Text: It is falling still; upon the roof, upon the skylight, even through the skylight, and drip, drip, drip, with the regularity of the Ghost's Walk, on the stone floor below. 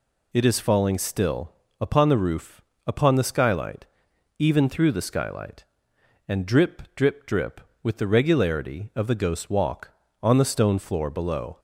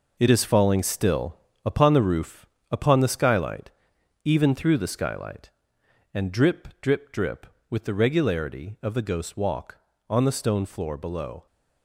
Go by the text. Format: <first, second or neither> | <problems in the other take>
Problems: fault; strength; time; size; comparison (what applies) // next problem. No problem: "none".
first | gets quieter; strong; throughout; 9 dB